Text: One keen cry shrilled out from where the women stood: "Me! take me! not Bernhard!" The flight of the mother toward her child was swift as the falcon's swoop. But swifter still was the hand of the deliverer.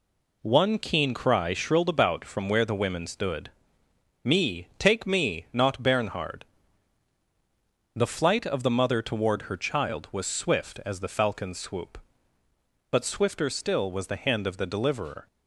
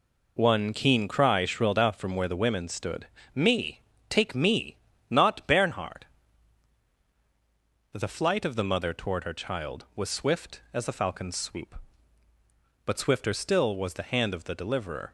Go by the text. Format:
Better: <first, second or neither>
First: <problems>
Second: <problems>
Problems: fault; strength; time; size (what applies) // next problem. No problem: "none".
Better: second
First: says "about" for "out"; at 1.8 s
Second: none